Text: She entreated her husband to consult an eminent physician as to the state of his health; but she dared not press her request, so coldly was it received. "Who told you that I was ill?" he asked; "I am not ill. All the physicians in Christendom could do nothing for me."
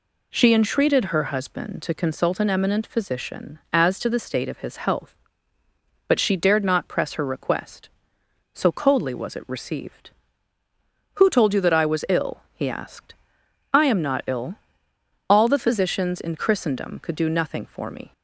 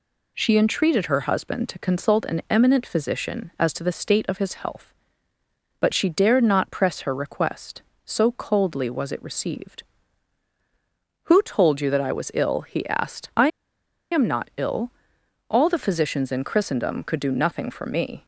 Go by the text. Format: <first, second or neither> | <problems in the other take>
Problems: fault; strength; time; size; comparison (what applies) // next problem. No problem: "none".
first | pauses between "I" and "am"; noticeable; at 13.4 s; 0.64 s long